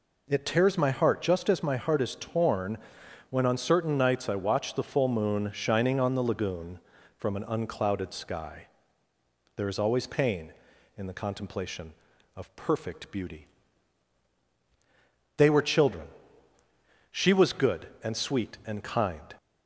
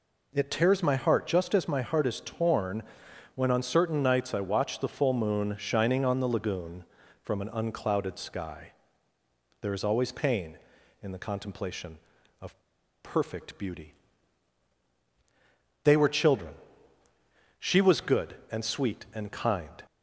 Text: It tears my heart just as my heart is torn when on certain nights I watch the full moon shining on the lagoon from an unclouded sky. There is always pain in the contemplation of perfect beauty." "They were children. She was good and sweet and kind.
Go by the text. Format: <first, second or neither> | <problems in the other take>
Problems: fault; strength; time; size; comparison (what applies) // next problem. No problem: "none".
first | pauses between "torn" and "when"; noticeable; at 2.8 s; 0.50 s long; noticeable in the first // pauses between "of" and "perfect"; at 12.5 s; 0.43 s long